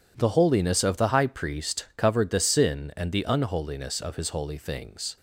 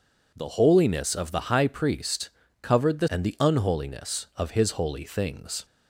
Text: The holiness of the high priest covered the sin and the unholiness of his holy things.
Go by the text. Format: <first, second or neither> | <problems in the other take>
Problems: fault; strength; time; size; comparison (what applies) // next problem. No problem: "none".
first | pauses between "priest" and "covered"; slight; at 2.2 s; 0.32 s long // skips "sin"; at 3.0 s